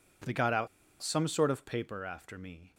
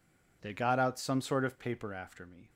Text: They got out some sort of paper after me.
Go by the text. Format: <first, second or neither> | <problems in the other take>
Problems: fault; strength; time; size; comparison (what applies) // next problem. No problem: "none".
second | pauses between "out" and "some"; slight; at 0.6 s; 0.34 s long